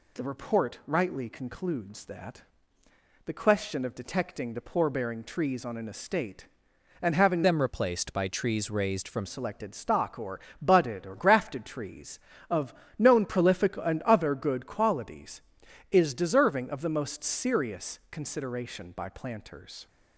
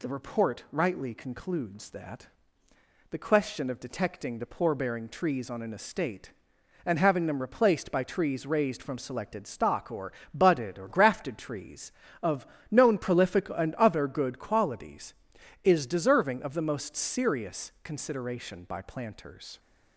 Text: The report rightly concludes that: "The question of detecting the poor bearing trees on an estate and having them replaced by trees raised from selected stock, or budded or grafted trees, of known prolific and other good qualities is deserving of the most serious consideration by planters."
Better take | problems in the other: second | changes voice from "them" to "from"; from 7.4 to 9.2 s; 1.8 s long // pauses between "or" and "budded"; slight; at 10.4 s; 0.20 s long; slight in the second // pauses between "of" and "known"; slight; at 12.7 s; 0.26 s long; slight in the second

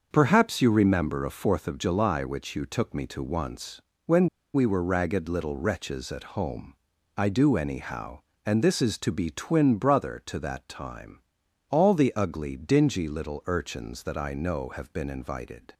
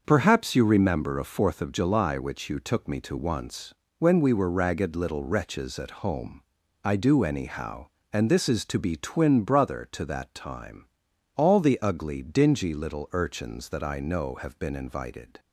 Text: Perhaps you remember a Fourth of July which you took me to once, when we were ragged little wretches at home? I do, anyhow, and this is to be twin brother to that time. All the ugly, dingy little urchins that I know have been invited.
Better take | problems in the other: second | starts louder than the rest; until 1.1 s; 6.5 dB; also in the second // pauses between "when" and "we"; slight; at 4.2 s; 0.26 s long

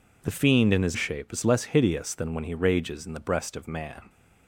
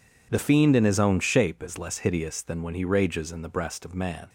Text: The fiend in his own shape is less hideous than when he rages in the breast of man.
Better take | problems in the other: second | skips "own"; at 0.9 s

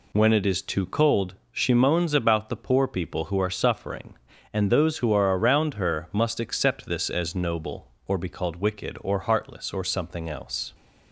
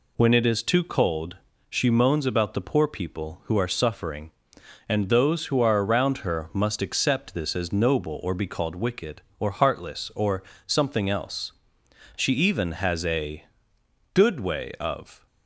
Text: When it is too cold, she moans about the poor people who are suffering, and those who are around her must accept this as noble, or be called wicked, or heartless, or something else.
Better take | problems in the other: first | pauses between "or" and "something"; slight; at 10.4 s; 0.24 s long // goes on to say "She even has a Good way of"; strong; from 12.1 s on; 3.1 s long

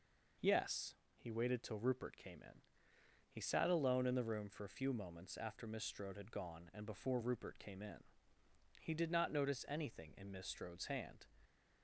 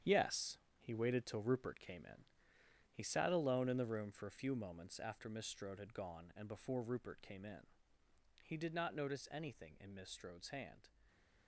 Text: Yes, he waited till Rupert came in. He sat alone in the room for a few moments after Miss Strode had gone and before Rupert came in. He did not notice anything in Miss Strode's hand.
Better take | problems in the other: first | gets quieter; strong; throughout; 9 dB // stays silent after the last word; slight; from 10.8 s on; 0.6 s long

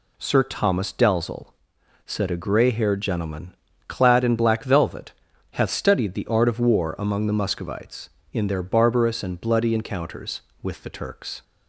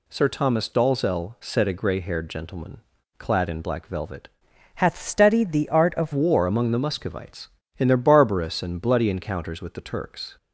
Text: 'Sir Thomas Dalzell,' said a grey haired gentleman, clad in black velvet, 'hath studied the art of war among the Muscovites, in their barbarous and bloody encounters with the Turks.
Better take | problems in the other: first | changes voice from "hath" to "of"; from 4.7 to 6.1 s; 1.4 s long

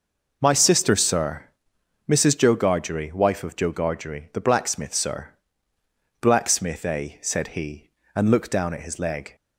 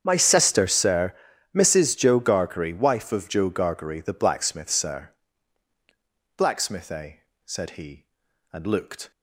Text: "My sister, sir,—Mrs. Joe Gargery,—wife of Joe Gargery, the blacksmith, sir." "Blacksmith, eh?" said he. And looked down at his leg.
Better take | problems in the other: first | starts louder than the rest; strong; until 1.0 s; 8 dB // stops before "down at his leg"; at 9.1 s

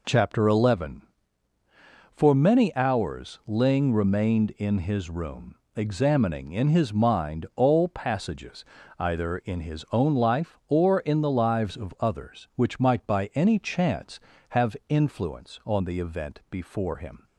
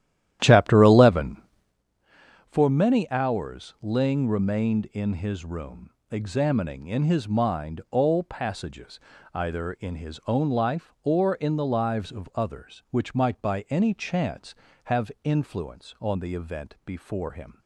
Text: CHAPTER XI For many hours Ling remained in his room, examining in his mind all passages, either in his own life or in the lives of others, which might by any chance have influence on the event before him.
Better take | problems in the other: first | starts louder than the rest; strong; until 1.8 s; 12 dB

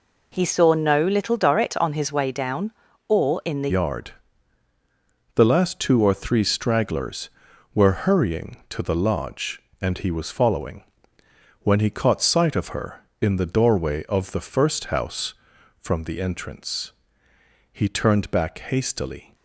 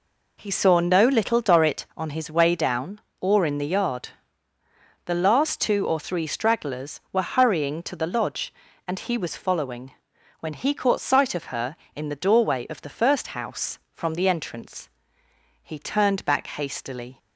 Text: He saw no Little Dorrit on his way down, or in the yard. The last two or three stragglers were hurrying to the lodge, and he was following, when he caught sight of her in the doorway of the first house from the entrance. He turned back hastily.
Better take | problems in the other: second | changes voice at "yard"; from 3.6 s on; 15.7 s long

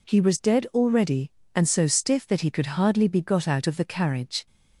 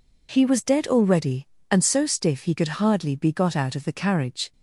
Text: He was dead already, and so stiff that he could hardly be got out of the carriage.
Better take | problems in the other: first | skips "that"; at 2.4 s

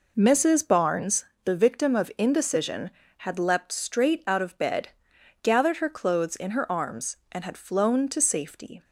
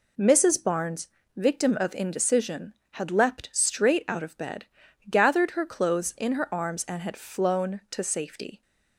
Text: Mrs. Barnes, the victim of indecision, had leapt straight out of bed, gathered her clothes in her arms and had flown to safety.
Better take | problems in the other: first | skips "the"; at 1.2 s

